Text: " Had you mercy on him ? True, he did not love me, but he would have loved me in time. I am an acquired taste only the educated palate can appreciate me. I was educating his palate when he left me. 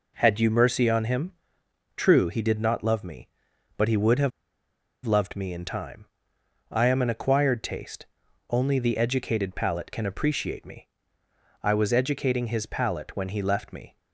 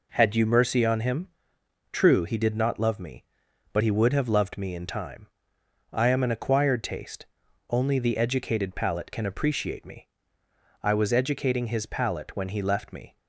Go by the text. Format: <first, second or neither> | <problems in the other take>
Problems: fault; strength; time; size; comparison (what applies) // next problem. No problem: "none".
second | pauses between "have" and "loved"; noticeable; at 4.3 s; 0.74 s long // pauses between "taste" and "only"; at 8.0 s; 0.44 s long; also in the second